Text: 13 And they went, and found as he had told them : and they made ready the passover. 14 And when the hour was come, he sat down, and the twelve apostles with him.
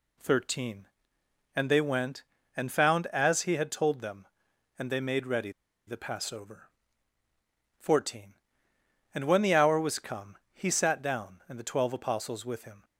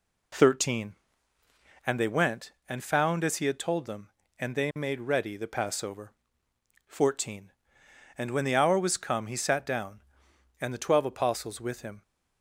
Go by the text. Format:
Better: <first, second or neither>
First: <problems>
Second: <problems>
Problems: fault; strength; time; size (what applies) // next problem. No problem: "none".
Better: second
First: pauses between "ready" and "the"; slight; at 5.5 s; 0.35 s long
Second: none